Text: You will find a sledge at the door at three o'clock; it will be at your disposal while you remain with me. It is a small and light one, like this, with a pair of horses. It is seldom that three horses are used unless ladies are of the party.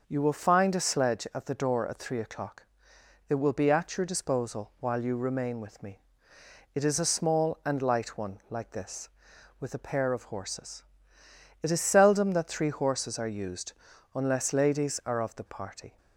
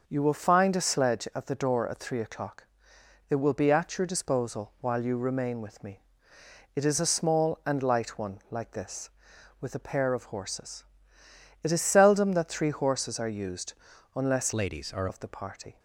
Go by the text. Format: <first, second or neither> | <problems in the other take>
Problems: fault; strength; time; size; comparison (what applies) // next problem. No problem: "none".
first | pauses between "used" and "unless"; at 13.7 s; 0.42 s long; also in the first // changes voice from "ladies" to "are"; from 14.5 to 15.0 s; 0.5 s long